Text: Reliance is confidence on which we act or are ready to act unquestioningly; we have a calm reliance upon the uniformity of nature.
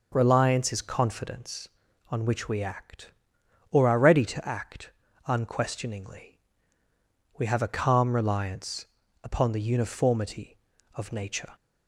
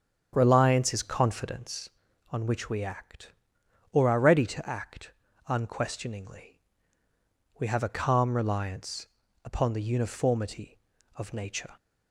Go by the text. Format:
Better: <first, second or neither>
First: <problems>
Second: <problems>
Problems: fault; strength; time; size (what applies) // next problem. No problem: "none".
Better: first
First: pauses between "act" and "unquestioningly"; slight; at 4.9 s; 0.34 s long // pauses between "reliance" and "upon"; at 8.8 s; 0.38 s long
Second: starts louder than the rest; strong; until 2.0 s; 8 dB // pauses between "act" and "unquestioningly"; slight; at 5.1 s; 0.34 s long // pauses between "reliance" and "upon"; at 9.0 s; 0.38 s long